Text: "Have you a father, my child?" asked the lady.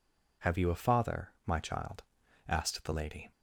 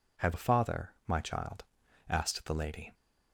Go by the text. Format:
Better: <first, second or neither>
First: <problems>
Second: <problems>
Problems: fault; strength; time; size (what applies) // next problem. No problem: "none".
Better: first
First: none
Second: skips "you"; at 0.3 s